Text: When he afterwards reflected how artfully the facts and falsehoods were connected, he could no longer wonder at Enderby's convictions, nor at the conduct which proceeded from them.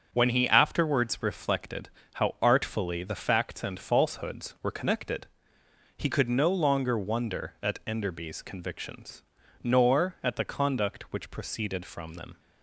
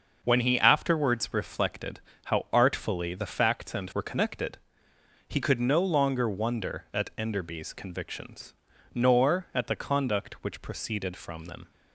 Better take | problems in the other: first | starts louder than the rest; until 1.2 s; 6 dB; also in the first // pauses between "reflected" and "how"; slight; at 1.9 s; 0.28 s long; slight in the first // skips "falsehoods"; at 3.9 s

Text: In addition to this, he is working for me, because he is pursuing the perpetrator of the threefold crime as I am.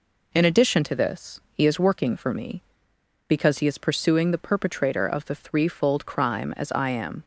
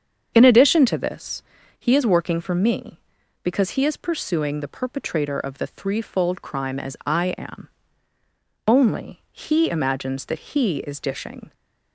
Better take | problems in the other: first | starts louder than the rest; strong; until 1.3 s; 7.5 dB // goes on to say "Only he imagines that he is dishing"; strong; from 8.6 s on; 2.8 s long

